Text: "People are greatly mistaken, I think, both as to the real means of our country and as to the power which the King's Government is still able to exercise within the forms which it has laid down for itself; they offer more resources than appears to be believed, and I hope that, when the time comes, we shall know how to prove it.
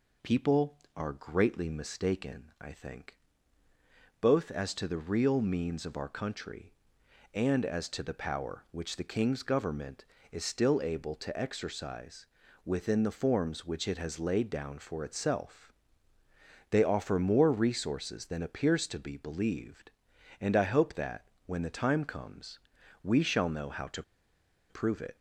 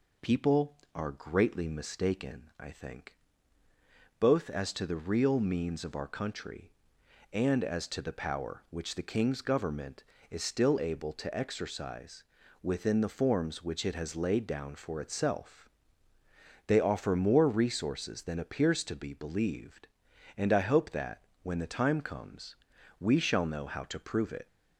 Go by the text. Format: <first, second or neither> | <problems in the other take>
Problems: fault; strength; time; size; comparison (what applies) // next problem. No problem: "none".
second | pauses between "exercise" and "within"; at 12.2 s; 0.40 s long; also in the second // pauses between "to" and "prove"; noticeable; at 24.0 s; 0.67 s long